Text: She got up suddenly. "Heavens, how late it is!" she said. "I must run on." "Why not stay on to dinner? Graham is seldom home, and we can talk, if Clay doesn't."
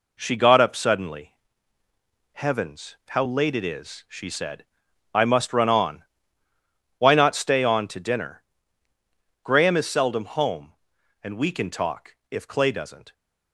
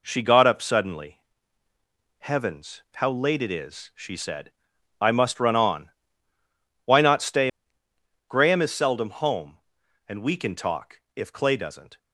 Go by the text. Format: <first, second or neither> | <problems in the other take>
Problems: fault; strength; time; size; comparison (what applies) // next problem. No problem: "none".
first | skips "on to dinner"; at 7.8 s